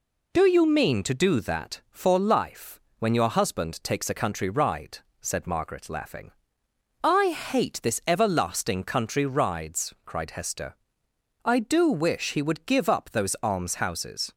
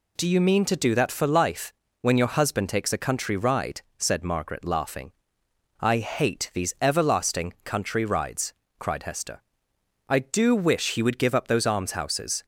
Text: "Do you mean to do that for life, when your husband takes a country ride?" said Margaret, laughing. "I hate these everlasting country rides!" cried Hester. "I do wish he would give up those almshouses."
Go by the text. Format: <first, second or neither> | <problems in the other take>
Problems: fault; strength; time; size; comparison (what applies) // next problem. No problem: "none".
second | says "this" for "these"; at 7.8 s